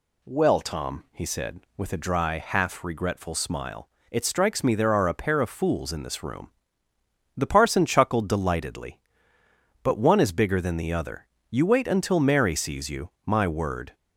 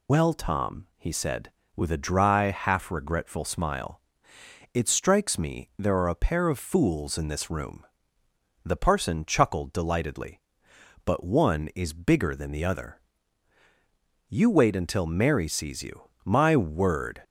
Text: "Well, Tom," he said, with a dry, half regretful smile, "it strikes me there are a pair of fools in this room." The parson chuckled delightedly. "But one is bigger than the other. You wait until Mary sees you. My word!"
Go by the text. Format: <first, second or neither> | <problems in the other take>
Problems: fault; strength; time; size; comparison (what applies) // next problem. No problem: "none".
first | loses the start of "Well"; at 0.0 s; 105 ms